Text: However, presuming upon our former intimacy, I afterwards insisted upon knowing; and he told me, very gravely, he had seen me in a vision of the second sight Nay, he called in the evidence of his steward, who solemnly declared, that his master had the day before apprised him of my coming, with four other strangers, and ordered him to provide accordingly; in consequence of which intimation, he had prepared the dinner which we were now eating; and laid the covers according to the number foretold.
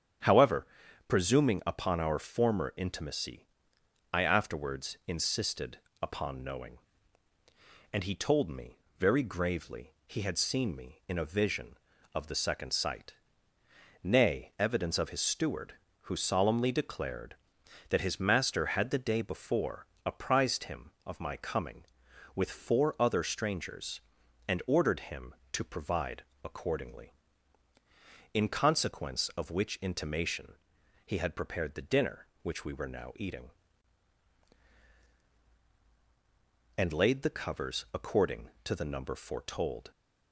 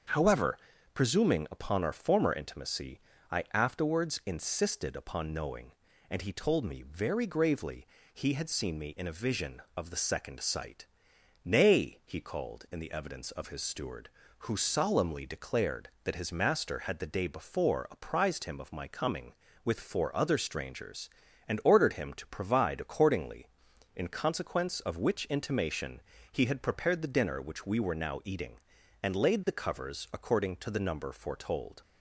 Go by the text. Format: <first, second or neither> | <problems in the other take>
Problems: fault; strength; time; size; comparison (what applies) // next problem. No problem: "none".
second | starts louder than the rest; strong; until 1.6 s; 9 dB; also in the second // pauses between "insisted" and "upon"; slight; at 5.7 s; 0.24 s long // pauses between "sight" and "Nay"; noticeable; at 13.1 s; 0.88 s long; noticeable in the second // skips "he called in the"; at 14.5 s // pauses between "before" and "apprised"; slight; at 19.8 s; 0.20 s long // pauses between "provide" and "accordingly"; slight; at 26.2 s; 0.20 s long